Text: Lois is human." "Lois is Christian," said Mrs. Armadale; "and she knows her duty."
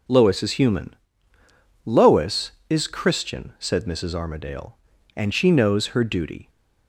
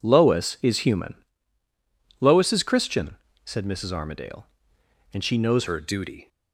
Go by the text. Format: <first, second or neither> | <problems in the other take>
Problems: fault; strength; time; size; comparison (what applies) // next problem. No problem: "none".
first | changes voice at "her"; from 5.6 s on; 0.6 s long